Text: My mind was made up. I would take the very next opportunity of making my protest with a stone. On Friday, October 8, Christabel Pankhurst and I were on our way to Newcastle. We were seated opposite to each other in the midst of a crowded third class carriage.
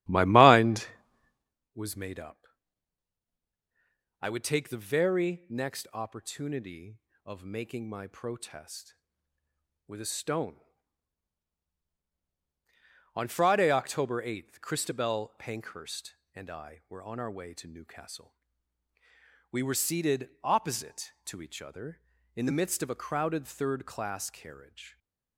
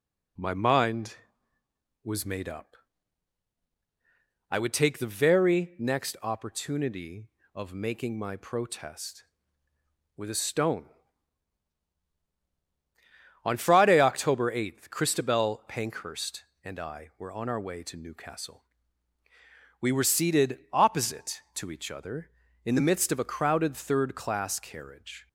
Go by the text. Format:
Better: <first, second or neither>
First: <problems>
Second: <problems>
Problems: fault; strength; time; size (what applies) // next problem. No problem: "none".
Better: second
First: starts louder than the rest; strong; until 1.6 s; 12.5 dB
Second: none